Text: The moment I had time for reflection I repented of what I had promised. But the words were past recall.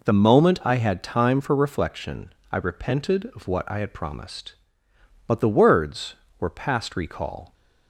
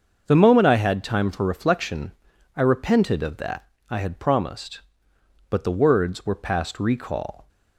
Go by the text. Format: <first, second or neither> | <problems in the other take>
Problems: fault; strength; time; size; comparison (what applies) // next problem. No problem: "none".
first | starts louder than the rest; until 1.2 s; 6.5 dB // pauses between "reflection" and "I"; noticeable; at 2.1 s; 0.46 s long; slight in the first // says "that" for "what"; at 3.3 s